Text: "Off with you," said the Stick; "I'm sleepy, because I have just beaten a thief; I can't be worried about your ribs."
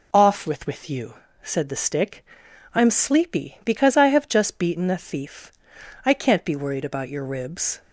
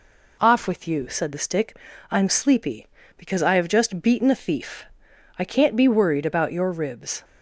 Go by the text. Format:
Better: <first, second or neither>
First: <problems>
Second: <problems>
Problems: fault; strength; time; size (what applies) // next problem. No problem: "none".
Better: second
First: says "with" twice; at 0.6 s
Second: none